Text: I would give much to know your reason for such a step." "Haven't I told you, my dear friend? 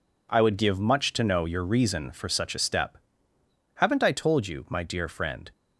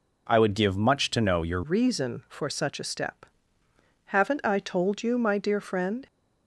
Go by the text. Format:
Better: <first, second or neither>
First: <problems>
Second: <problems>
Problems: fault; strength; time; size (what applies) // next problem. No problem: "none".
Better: first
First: none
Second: changes voice at "reason"; from 1.6 s on; 4.4 s long